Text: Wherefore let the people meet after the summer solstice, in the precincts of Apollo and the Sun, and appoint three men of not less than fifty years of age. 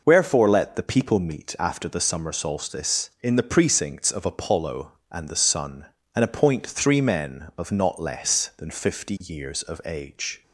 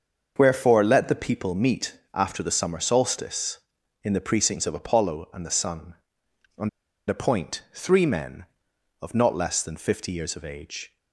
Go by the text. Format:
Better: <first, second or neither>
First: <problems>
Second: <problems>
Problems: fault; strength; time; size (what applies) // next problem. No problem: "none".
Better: first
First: none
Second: starts louder than the rest; until 1.3 s; 6.5 dB // pauses between "and" and "appoint"; at 6.6 s; 0.39 s long